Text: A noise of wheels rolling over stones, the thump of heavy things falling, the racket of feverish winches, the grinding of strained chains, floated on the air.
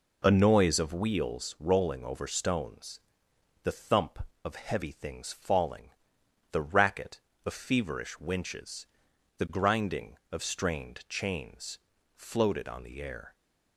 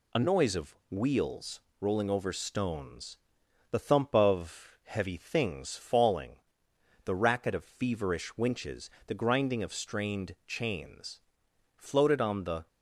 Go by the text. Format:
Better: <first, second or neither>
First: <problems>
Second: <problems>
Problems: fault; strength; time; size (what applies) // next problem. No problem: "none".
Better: first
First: none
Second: pauses between "of" and "wheels"; slight; at 0.7 s; 0.16 s long // pauses between "wheels" and "rolling"; slight; at 1.5 s; 0.22 s long // stops before "air"; at 12.6 s